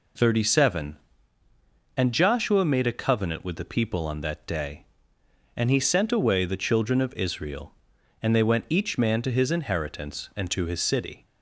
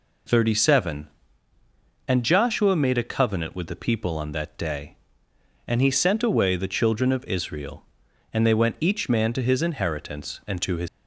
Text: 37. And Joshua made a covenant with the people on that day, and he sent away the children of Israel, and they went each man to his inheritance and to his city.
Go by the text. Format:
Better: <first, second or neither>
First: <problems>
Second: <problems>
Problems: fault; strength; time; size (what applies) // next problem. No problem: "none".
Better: first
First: none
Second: stops before "city"; at 10.8 s